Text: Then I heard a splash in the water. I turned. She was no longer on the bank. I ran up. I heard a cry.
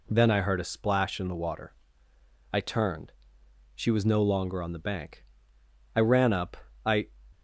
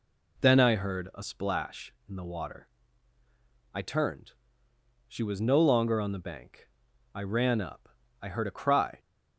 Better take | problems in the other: second | stops before "heard a cry"; at 7.3 s

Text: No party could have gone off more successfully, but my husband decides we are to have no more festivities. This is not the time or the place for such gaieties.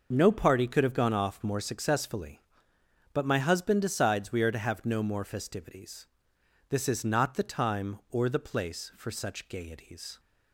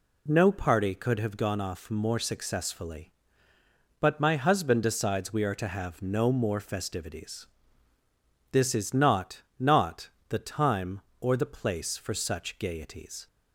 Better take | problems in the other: first | says "not" twice; at 9.5 s

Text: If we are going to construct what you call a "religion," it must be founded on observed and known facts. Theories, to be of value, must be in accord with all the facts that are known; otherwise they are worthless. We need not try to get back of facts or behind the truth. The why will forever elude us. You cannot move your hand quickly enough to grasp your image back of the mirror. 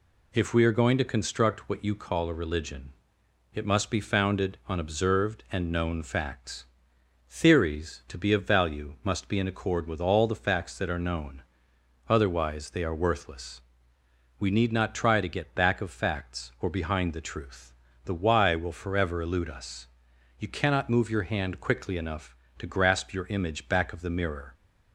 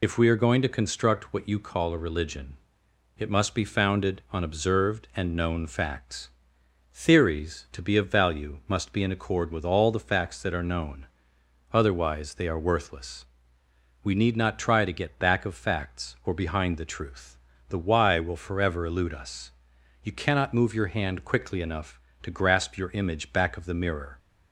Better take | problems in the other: first | loses the start of "If"; at 0.0 s; 50 ms

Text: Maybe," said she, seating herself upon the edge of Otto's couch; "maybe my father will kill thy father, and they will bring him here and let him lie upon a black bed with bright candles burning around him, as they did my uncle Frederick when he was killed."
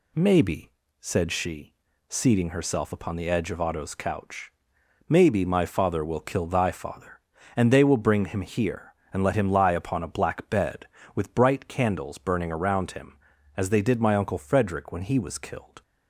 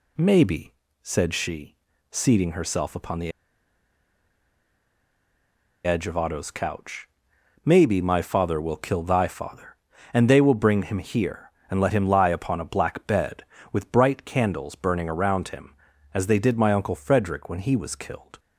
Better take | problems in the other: first | pauses between "the" and "edge"; strong; at 3.3 s; 2.5 s long

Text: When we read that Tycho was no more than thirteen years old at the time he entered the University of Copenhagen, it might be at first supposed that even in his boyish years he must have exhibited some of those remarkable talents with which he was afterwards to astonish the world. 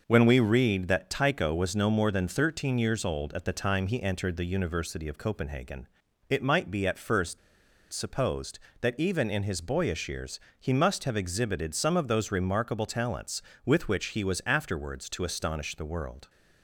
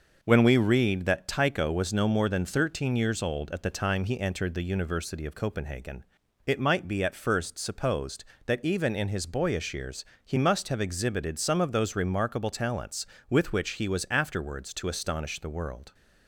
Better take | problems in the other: second | pauses between "first" and "supposed"; noticeable; at 7.3 s; 0.53 s long // pauses between "years" and "he"; slight; at 10.3 s; 0.18 s long; slight in the second

